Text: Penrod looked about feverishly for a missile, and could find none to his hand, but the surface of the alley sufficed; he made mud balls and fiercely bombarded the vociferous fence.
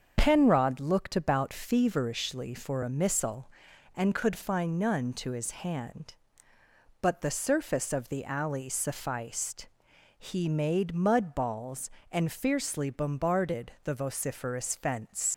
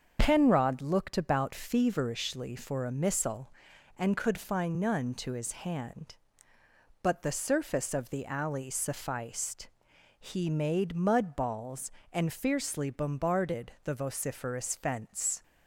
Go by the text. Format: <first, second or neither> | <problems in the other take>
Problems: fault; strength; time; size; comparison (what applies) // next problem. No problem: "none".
second | starts louder than the rest; until 1.1 s; 7 dB; also in the second // leaves "fence" unfinished; at 15.3 s; 80 ms